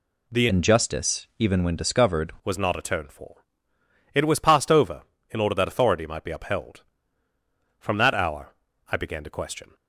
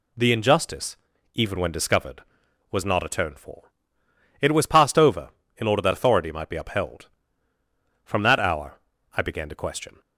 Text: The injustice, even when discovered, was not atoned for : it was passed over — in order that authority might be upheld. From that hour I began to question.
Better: second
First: changes voice from "injustice" to "discovered"; from 0.4 to 2.3 s; 1.9 s long // pauses between "hour" and "I"; slight; at 8.5 s; 0.36 s long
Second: pauses between "hour" and "I"; slight; at 8.7 s; 0.36 s long

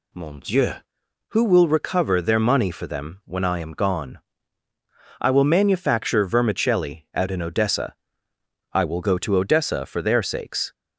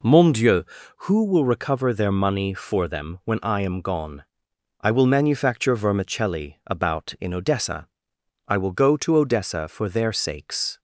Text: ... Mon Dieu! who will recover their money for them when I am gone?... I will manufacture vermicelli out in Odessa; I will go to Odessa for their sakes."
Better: first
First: none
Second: says "about" for "out"; at 6.6 s

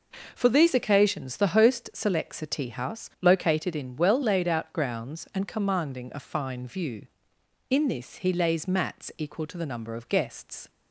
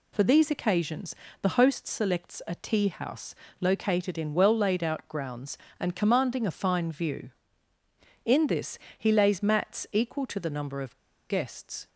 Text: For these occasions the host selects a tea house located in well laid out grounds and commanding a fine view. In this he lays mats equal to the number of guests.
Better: first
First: none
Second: pauses between "occasions" and "the"; slight; at 1.1 s; 0.26 s long // pauses between "house" and "located"; slight; at 3.3 s; 0.26 s long // pauses between "this" and "he"; slight; at 8.7 s; 0.18 s long // pauses between "of" and "guests"; slight; at 10.9 s; 0.33 s long

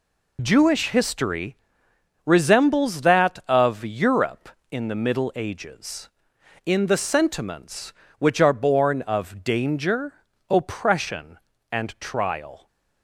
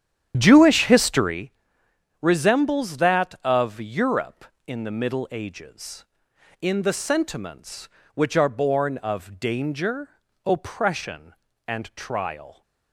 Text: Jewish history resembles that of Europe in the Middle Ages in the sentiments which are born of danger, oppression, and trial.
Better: first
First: pauses between "history" and "resembles"; noticeable; at 1.5 s; 0.70 s long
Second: starts louder than the rest; strong; until 1.4 s; 9.5 dB // pauses between "history" and "resembles"; noticeable; at 1.5 s; 0.70 s long

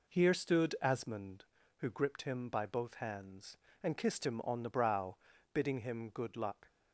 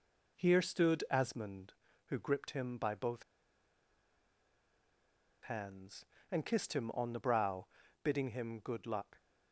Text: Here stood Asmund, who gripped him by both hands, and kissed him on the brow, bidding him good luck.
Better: first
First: none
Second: pauses between "both" and "hands"; strong; at 3.2 s; 2.2 s long

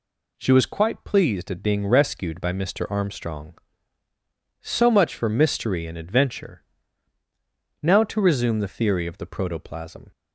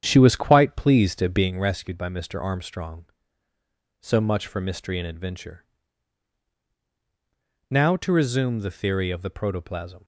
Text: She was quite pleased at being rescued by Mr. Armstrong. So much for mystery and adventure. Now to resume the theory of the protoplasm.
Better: first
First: none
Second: starts louder than the rest; strong; until 1.5 s; 9 dB

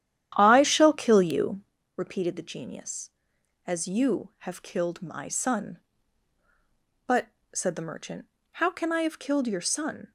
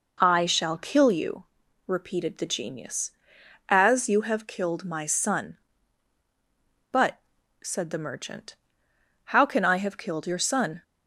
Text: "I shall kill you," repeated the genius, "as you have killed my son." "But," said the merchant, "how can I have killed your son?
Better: second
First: starts louder than the rest; strong; until 1.8 s; 11 dB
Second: none

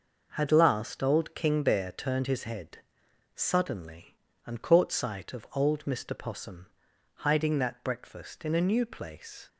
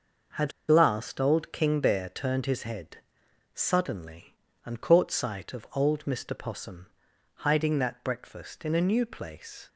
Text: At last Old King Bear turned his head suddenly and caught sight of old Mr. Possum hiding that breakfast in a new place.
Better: first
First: pauses between "head" and "suddenly"; noticeable; at 2.7 s; 0.56 s long // pauses between "Possum" and "hiding"; noticeable; at 6.6 s; 0.48 s long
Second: pauses between "At" and "last"; slight; at 0.5 s; 0.18 s long // pauses between "head" and "suddenly"; noticeable; at 2.9 s; 0.56 s long // pauses between "Possum" and "hiding"; noticeable; at 6.8 s; 0.48 s long

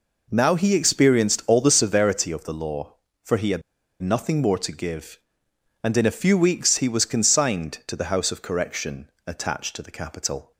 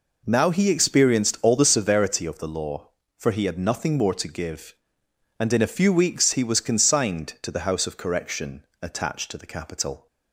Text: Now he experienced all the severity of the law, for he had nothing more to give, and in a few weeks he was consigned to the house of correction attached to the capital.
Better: second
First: pauses between "had" and "nothing"; at 3.6 s; 0.41 s long // pauses between "correction" and "attached"; slight; at 9.0 s; 0.16 s long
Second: pauses between "correction" and "attached"; slight; at 8.6 s; 0.16 s long

